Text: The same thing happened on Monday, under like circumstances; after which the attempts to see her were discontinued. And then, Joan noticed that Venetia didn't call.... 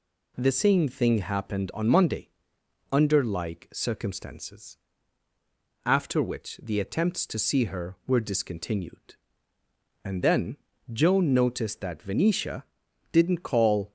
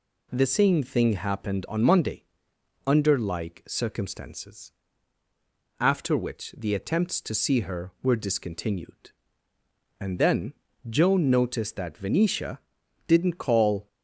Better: neither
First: pauses between "Venetia" and "didn't"; noticeable; at 12.6 s; 0.48 s long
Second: pauses between "Venetia" and "didn't"; noticeable; at 12.5 s; 0.48 s long

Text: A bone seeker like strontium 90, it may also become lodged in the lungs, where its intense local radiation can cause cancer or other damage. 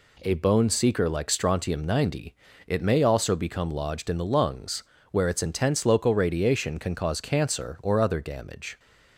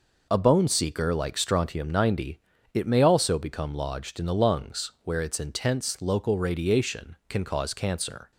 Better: first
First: none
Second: stops before "or other damage"; at 8.3 s

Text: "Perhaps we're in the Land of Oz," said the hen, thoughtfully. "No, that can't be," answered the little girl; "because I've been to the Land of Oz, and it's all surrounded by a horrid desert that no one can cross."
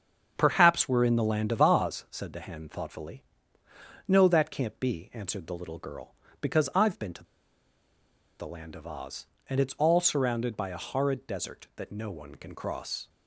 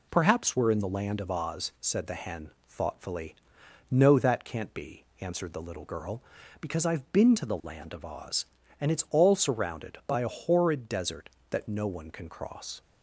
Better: second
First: starts louder than the rest; until 1.3 s; 7 dB // pauses between "to" and "the"; at 7.2 s; 1.1 s long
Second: none

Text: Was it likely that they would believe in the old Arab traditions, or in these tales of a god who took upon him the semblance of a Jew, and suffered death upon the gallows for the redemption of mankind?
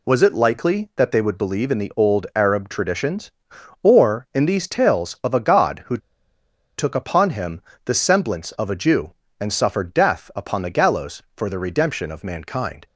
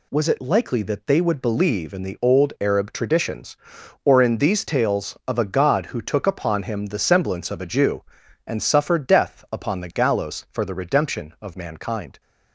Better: second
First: pauses between "who" and "took"; noticeable; at 5.9 s; 0.80 s long // pauses between "him" and "the"; slight; at 7.6 s; 0.24 s long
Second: none

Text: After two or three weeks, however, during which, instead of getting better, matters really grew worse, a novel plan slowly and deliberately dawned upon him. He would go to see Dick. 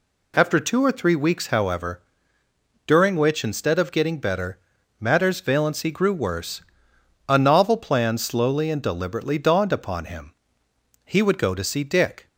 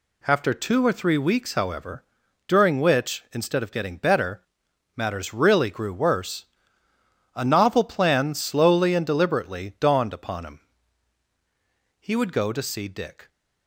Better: second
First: says "valency" for "really"; at 5.4 s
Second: none

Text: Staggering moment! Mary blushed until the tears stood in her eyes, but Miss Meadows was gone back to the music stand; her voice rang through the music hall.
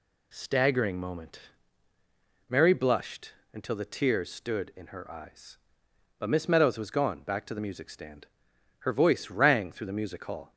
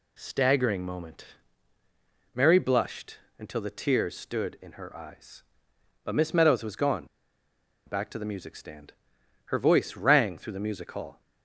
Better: first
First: pauses between "blushed" and "until"; slight; at 3.3 s; 0.18 s long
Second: pauses between "blushed" and "until"; slight; at 3.1 s; 0.18 s long // pauses between "gone" and "back"; noticeable; at 7.0 s; 0.81 s long

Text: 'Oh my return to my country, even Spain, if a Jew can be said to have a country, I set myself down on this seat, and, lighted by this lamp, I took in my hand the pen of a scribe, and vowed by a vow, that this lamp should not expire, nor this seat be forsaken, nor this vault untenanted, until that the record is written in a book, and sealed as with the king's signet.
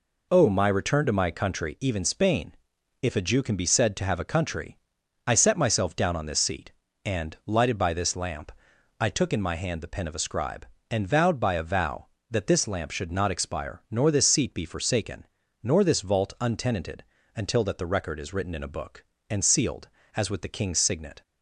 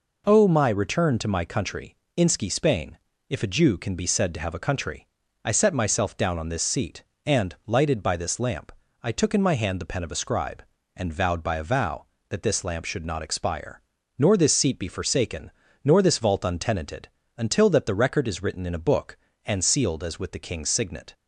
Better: first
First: none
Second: says "inski" for "even"; at 2.1 s

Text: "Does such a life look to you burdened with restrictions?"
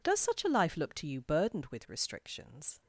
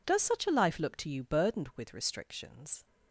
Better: neither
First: none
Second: none

